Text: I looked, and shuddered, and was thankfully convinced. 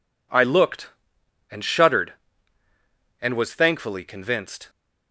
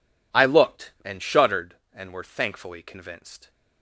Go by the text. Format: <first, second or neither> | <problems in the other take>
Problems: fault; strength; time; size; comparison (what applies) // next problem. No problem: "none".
first | says "were" for "was"; at 2.1 s